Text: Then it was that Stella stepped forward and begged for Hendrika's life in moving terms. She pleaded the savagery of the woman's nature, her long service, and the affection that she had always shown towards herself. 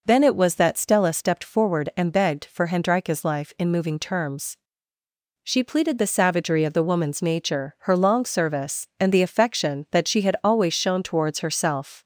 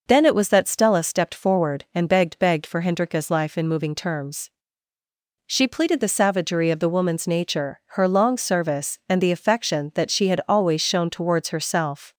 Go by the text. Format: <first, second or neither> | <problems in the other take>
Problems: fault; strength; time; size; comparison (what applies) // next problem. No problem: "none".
first | says "begged" twice; at 2.3 s